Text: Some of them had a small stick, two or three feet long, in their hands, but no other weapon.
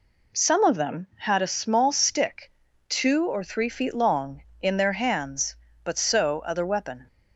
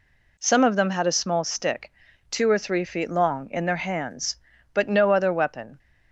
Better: second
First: says "so" for "no"; at 5.9 s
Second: none

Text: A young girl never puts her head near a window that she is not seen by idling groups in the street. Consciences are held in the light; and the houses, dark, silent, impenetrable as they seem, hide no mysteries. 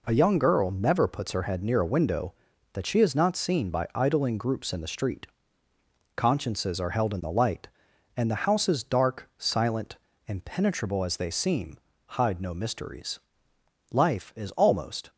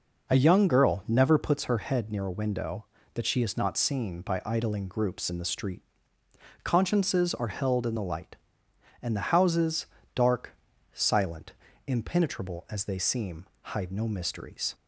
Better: second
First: goes on to say "Life is almost"; noticeable; from 13.8 s on; 1.2 s long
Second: none

